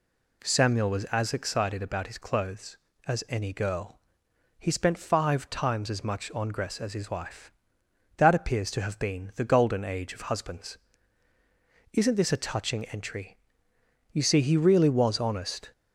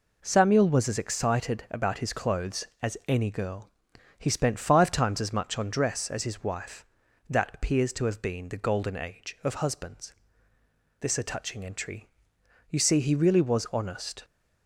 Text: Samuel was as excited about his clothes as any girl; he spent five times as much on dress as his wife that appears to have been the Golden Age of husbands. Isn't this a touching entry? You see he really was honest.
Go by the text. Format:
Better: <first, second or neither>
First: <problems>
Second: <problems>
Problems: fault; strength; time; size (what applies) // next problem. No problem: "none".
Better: first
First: none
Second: skips "Isn't"; at 10.5 s